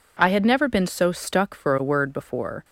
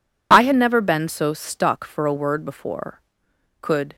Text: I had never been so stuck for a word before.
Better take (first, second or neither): first